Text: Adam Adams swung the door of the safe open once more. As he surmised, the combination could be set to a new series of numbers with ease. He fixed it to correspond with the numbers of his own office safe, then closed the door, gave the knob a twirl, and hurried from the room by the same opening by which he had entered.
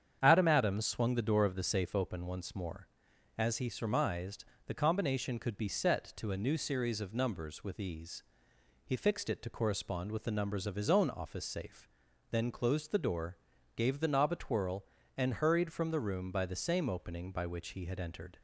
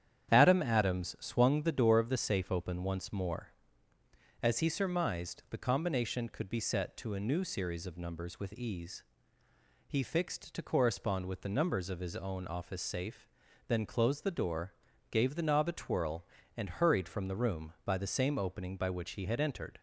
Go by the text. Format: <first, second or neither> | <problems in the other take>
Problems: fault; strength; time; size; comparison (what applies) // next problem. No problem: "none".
first | starts louder than the rest; strong; until 1.3 s; 9.5 dB; strong in the first // skips "it"; at 10.5 s